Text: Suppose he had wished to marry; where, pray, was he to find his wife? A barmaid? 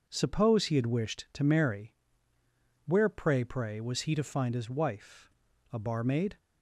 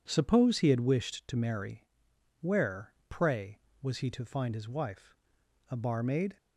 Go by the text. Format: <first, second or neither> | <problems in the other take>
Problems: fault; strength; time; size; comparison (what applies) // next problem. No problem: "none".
second | says "pray" twice; at 3.4 s